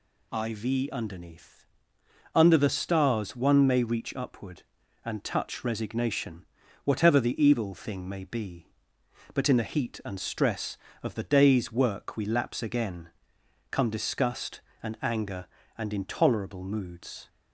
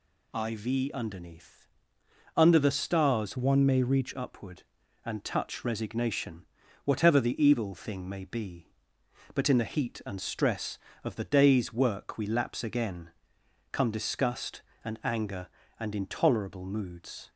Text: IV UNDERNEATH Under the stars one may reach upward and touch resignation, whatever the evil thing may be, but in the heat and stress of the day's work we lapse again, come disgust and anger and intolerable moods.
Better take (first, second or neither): first